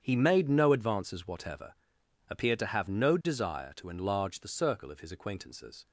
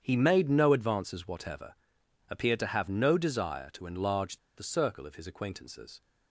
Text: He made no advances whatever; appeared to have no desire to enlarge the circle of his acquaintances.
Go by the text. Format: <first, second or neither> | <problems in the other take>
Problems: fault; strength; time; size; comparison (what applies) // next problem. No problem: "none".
first | starts louder than the rest; strong; until 1.0 s; 8.5 dB; strong in the first // pauses between "enlarge" and "the"; slight; at 4.3 s; 0.19 s long